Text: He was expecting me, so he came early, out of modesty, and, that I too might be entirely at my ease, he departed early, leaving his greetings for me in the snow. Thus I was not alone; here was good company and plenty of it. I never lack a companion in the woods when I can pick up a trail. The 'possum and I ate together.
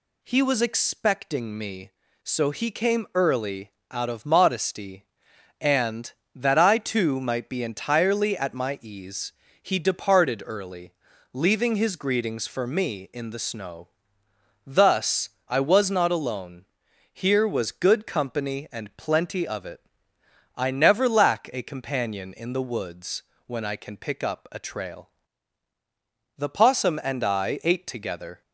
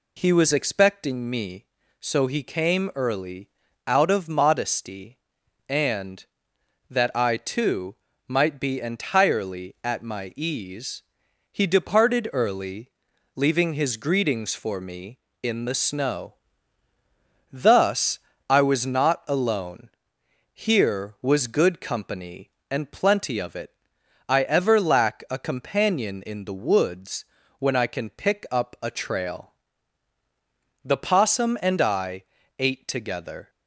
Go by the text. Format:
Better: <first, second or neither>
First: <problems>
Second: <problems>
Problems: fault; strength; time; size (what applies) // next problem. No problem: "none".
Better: first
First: pauses between "Thus" and "I"; slight; at 15.2 s; 0.18 s long // pauses between "woods" and "when"; slight; at 23.2 s; 0.24 s long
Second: pauses between "too" and "might"; slight; at 7.9 s; 0.34 s long // pauses between "Thus" and "I"; slight; at 18.1 s; 0.32 s long // says "ever" for "never"; at 24.4 s // pauses between "woods" and "when"; slight; at 27.2 s; 0.36 s long // pauses between "I" and "ate"; slight; at 32.2 s; 0.34 s long